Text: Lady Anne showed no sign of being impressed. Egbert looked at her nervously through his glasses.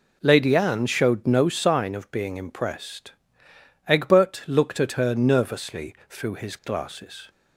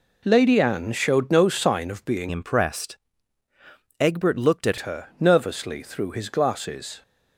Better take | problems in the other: first | changes voice from "impressed" to "at"; from 2.2 to 4.7 s; 2.5 s long

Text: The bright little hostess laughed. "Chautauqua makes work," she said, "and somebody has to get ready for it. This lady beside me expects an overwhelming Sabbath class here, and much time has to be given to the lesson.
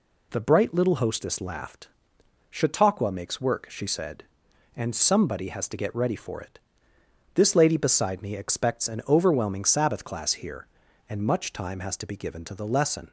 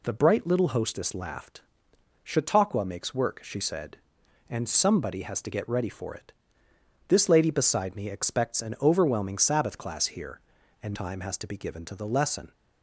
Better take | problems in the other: first | skips "much"; at 10.9 s

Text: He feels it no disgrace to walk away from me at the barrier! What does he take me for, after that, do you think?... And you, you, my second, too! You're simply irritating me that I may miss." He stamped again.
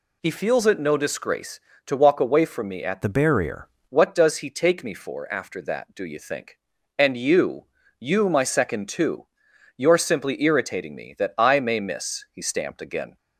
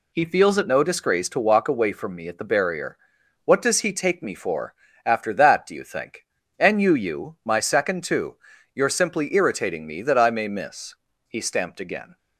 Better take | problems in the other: second | changes voice from "the" to "barrier"; from 3.0 to 3.6 s; 0.6 s long

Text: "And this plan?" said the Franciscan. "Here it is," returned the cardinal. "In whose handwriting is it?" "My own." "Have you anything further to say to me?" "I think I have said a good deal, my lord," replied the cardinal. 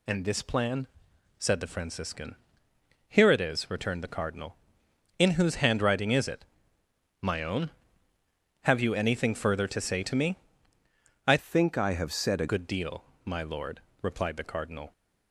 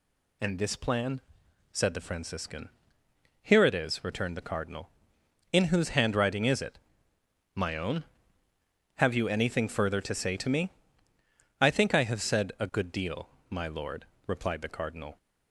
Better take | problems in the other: second | changes voice from "think" to "a"; from 11.3 to 12.4 s; 1.1 s long

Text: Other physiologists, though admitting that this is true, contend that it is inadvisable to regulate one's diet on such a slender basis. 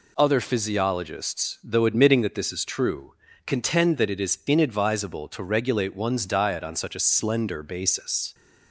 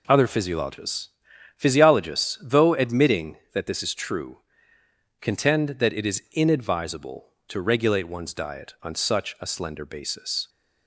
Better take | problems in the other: first | says "physiologists" twice; at 1.5 s

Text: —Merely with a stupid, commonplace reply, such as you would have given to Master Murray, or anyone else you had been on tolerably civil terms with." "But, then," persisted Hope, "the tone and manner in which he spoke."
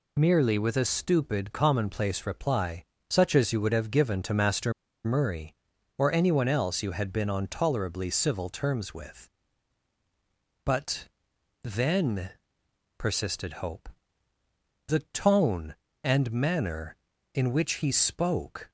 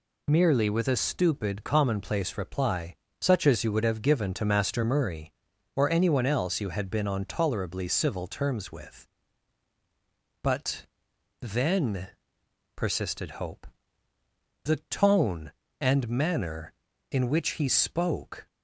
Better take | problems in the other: second | pauses between "Master" and "Murray"; slight; at 4.7 s; 0.33 s long

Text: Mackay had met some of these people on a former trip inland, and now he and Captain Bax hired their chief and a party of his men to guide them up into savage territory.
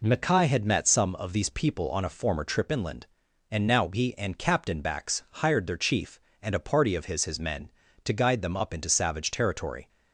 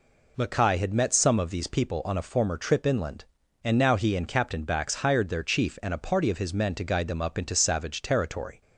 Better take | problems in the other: second | says "his" twice; at 7.2 s

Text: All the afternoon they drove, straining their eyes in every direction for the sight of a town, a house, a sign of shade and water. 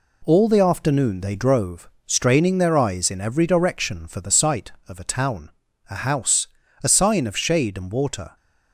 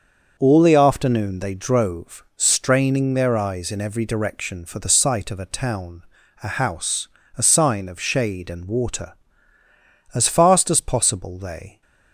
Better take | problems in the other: first | starts louder than the rest; until 1.3 s; 6.5 dB // goes on to say "As fast as possible they"; strong; from 10.1 s on; 1.6 s long

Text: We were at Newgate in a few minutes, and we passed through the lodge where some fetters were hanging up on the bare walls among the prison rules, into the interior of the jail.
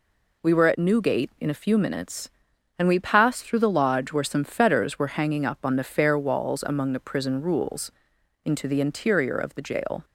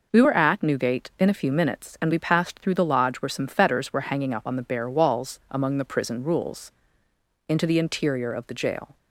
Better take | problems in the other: second | says "fair" for "bare"; at 5.8 s

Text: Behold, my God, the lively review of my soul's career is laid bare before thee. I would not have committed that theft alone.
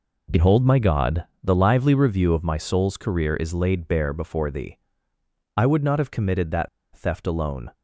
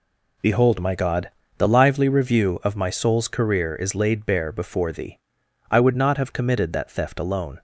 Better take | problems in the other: second | pauses between "that" and "theft"; slight; at 6.6 s; 0.26 s long

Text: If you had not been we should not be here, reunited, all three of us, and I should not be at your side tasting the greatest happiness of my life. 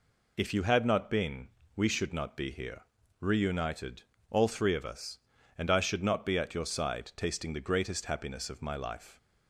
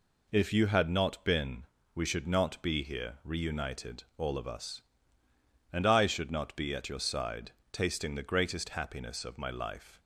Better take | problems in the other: first | pauses between "been" and "we"; slight; at 1.6 s; 0.30 s long; slight in the first // skips "three"; at 4.3 s // pauses between "side" and "tasting"; slight; at 7.5 s; 0.20 s long

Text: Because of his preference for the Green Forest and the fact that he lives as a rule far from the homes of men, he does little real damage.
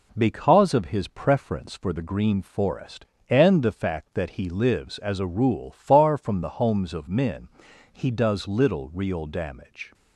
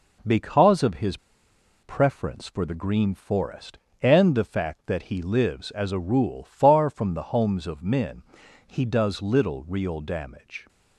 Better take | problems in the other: first | pauses between "his" and "preference"; noticeable; at 1.1 s; 0.66 s long

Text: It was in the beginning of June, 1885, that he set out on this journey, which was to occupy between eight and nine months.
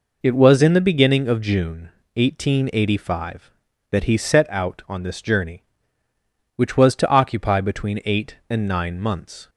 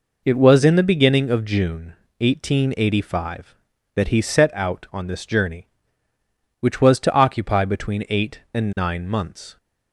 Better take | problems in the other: neither | none

